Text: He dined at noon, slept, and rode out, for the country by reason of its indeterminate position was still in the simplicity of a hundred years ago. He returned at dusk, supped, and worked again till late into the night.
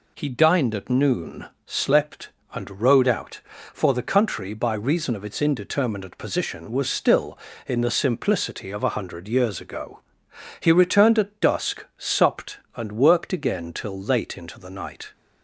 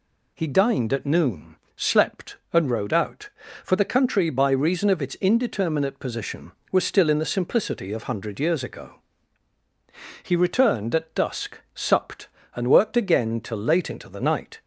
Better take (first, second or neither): first